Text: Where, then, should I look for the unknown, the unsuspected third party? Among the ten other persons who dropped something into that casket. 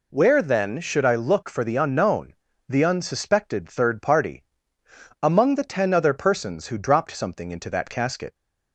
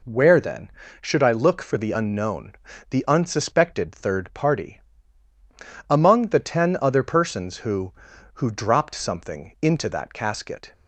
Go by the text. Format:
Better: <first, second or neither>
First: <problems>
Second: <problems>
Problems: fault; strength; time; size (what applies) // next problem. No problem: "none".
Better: first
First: none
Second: says "who" twice; at 8.3 s